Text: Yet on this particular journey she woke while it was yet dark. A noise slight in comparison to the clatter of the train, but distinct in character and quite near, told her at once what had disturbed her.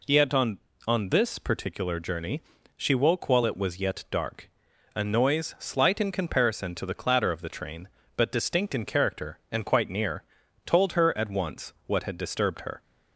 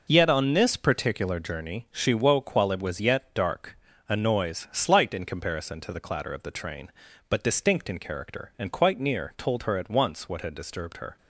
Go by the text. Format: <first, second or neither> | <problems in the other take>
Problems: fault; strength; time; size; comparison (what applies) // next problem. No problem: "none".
second | says "on" twice; at 0.8 s // pauses between "journey" and "she"; slight; at 2.4 s; 0.34 s long